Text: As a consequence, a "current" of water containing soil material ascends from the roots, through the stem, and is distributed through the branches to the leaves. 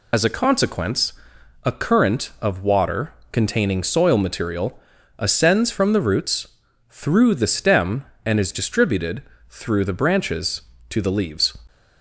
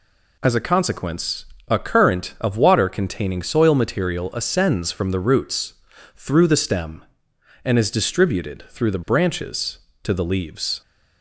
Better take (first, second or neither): second